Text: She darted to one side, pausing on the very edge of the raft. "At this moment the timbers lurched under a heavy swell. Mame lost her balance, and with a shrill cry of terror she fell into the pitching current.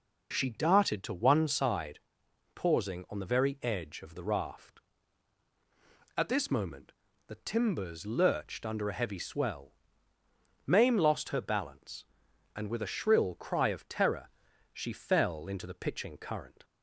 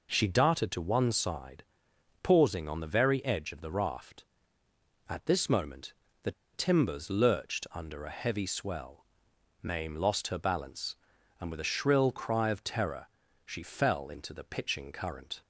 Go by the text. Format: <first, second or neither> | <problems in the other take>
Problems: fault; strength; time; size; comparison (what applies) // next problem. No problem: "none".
first | pauses between "moment" and "the"; slight; at 5.9 s; 0.30 s long; slight in the first // pauses between "the" and "timbers"; slight; at 6.3 s; 0.21 s long // pauses between "terror" and "she"; slight; at 13.0 s; 0.36 s long; also in the first